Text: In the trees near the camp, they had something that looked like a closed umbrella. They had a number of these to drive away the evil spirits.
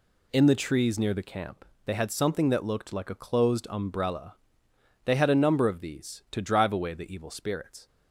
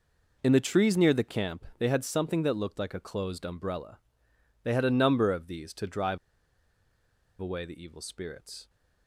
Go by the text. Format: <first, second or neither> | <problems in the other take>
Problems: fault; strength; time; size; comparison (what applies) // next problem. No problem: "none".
first | pauses between "drive" and "away"; at 6.1 s; 1.2 s long